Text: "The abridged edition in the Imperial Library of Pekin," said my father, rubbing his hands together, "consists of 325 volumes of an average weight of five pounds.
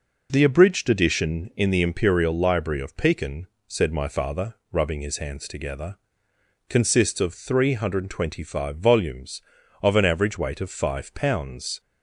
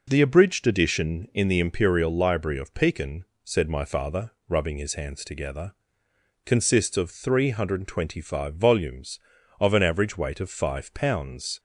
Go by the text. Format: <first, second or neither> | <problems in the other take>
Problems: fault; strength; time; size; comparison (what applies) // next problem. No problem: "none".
neither | none